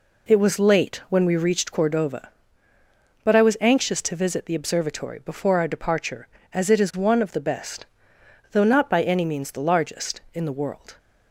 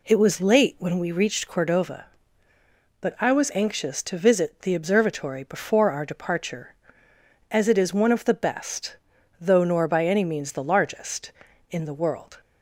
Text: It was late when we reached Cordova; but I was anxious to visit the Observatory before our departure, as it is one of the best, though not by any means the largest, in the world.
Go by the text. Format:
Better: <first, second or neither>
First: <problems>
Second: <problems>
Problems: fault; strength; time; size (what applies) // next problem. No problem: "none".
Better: first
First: none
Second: says "nor" for "not"; at 9.6 s